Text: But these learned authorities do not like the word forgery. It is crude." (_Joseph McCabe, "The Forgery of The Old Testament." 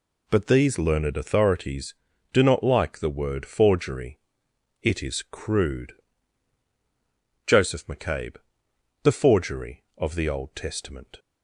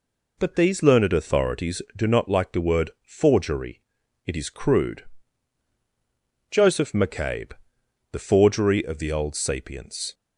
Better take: first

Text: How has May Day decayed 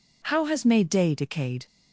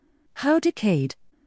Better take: first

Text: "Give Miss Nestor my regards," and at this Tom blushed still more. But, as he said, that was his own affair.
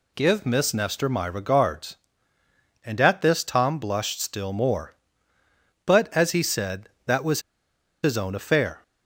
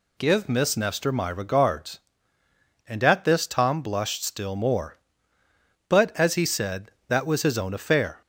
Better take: second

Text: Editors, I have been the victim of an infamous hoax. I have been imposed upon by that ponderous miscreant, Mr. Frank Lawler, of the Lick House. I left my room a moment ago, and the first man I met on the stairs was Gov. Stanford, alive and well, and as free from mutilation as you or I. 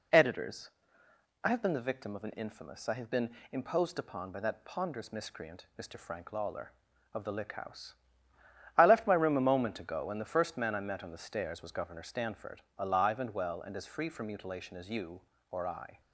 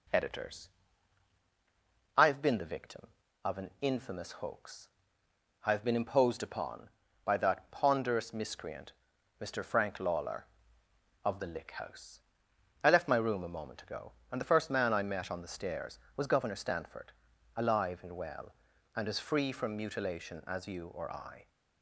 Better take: second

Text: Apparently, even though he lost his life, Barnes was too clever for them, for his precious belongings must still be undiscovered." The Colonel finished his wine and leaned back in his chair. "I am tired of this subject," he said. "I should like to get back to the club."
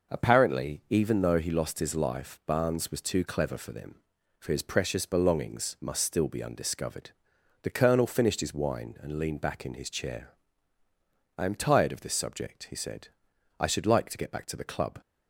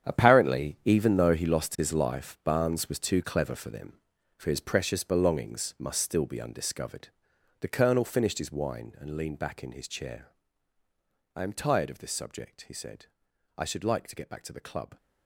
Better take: first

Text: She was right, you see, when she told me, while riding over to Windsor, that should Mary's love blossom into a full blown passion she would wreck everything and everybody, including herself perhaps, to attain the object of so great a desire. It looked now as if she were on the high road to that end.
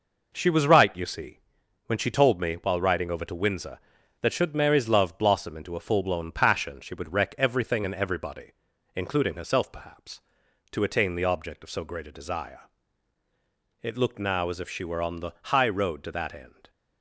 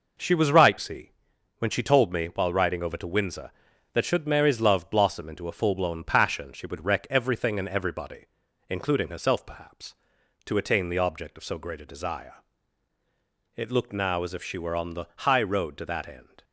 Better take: first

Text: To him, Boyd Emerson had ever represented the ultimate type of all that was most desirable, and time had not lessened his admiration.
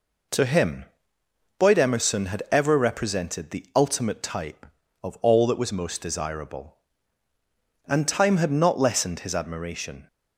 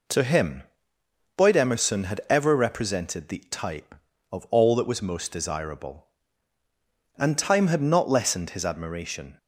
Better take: first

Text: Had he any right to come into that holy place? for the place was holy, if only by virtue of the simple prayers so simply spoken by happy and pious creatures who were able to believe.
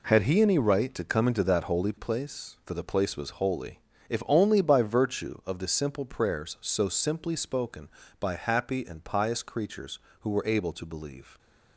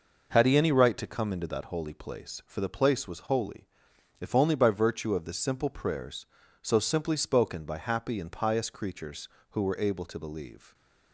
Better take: neither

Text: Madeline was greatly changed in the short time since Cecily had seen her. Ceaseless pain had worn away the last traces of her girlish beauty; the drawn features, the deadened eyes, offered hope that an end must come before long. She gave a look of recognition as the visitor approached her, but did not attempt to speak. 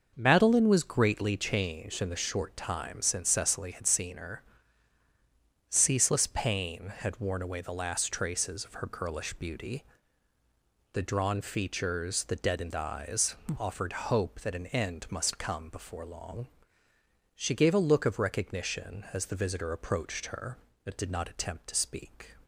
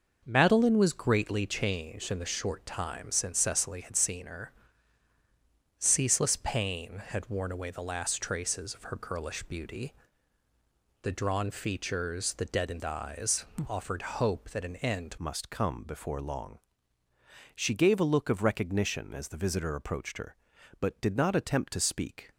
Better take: first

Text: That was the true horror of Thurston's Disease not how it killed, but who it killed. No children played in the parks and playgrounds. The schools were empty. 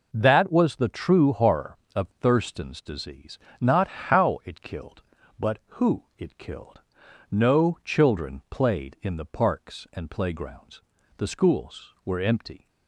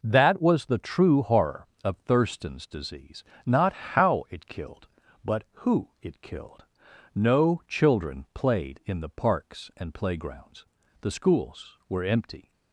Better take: neither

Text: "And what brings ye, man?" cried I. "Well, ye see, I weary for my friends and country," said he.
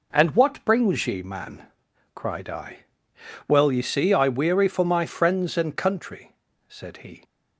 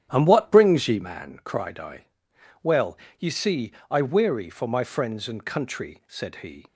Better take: first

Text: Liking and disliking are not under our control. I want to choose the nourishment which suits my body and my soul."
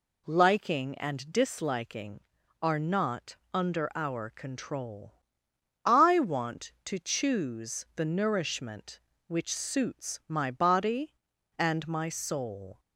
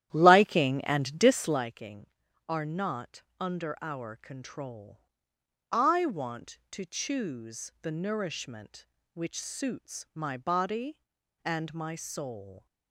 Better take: first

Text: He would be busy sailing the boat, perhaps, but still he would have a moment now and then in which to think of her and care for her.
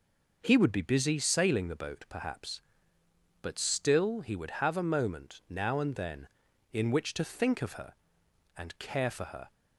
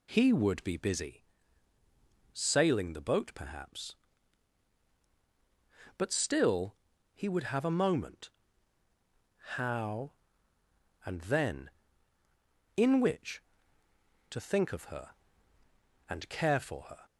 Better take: first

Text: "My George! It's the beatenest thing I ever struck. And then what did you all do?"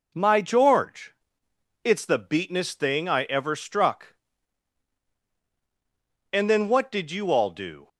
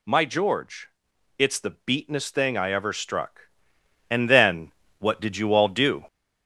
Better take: first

